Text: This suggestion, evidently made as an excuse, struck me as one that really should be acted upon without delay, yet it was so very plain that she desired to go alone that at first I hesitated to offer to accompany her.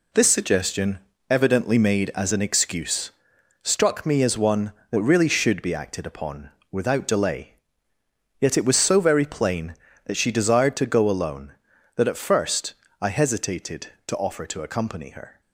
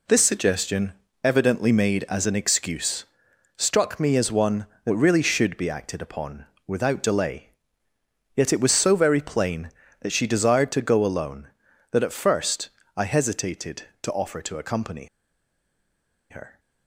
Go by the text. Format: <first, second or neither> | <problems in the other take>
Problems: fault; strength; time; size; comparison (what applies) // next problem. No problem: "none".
first | pauses between "upon" and "without"; slight; at 6.4 s; 0.22 s long; slight in the first // pauses between "first" and "I"; slight; at 12.6 s; 0.26 s long; slight in the first // pauses between "accompany" and "her"; at 15.0 s; 1.2 s long